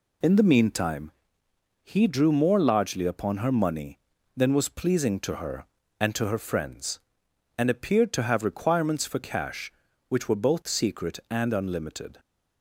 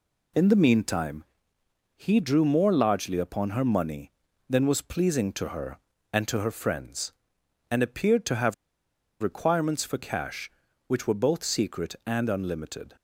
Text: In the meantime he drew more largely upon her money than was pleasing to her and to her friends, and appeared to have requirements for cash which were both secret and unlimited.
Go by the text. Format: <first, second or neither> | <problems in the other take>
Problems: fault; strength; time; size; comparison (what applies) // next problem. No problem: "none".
first | pauses between "meantime" and "he"; noticeable; at 1.2 s; 0.72 s long; noticeable in the first // pauses between "have" and "requirements"; noticeable; at 8.5 s; 0.66 s long